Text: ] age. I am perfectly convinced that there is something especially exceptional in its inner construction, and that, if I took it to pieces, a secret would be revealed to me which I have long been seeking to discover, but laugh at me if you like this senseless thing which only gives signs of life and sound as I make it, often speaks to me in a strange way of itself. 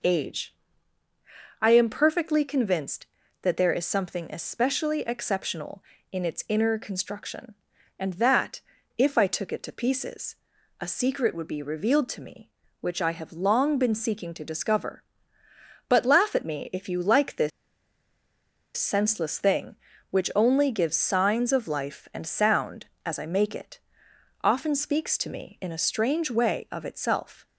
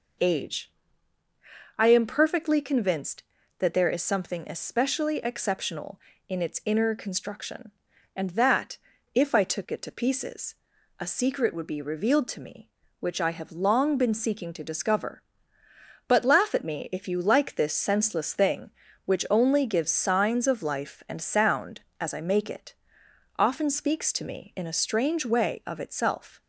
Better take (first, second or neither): second